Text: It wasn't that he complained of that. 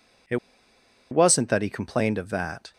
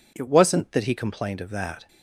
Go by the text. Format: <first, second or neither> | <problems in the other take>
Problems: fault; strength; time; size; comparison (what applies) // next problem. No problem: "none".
second | pauses between "It" and "wasn't"; noticeable; at 0.3 s; 0.74 s long